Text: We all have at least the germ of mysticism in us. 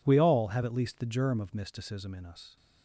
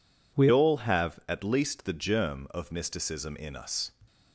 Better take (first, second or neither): first